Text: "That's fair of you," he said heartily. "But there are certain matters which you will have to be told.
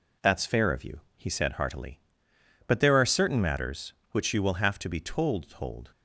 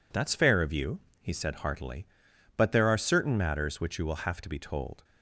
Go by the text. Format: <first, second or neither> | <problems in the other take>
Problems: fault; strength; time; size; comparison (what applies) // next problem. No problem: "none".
second | says "told" twice; at 5.4 s